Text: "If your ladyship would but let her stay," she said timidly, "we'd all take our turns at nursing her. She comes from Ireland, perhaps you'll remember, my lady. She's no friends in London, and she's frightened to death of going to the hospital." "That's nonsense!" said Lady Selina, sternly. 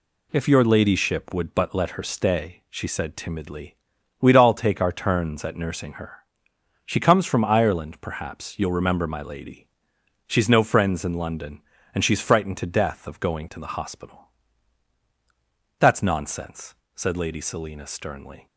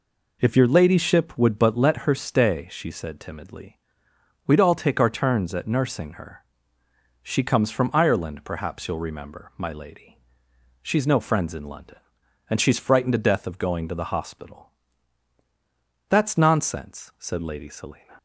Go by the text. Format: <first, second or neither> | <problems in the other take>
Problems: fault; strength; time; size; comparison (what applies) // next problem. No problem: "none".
first | stops before "sternly"; at 18.1 s